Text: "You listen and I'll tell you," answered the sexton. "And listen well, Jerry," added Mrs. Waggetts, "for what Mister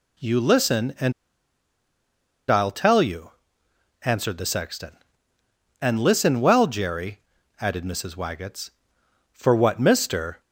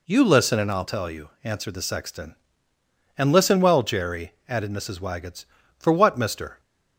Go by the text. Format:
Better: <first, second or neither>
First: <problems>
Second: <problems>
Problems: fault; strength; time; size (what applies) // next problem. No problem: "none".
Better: second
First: pauses between "and" and "I'll"; strong; at 1.1 s; 1.3 s long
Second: none